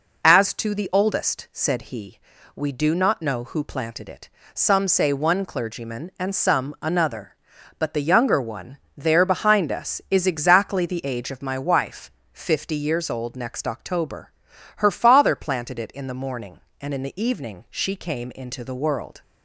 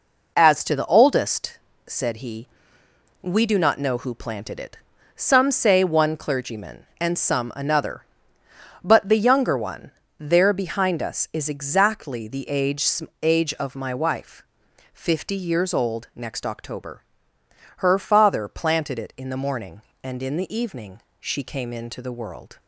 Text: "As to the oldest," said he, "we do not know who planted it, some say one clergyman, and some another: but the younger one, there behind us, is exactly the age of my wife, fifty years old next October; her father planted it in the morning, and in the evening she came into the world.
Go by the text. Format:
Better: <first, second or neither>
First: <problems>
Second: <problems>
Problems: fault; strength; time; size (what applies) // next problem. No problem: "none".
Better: first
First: none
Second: says "age" twice; at 13.2 s // pauses between "evening" and "she"; slight; at 21.0 s; 0.18 s long